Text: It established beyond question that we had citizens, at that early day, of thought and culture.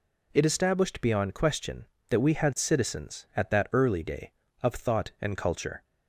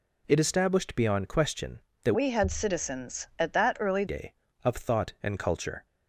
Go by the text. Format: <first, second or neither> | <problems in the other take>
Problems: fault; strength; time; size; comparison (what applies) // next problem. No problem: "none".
first | changes voice from "we" to "early"; from 2.1 to 4.0 s; 1.9 s long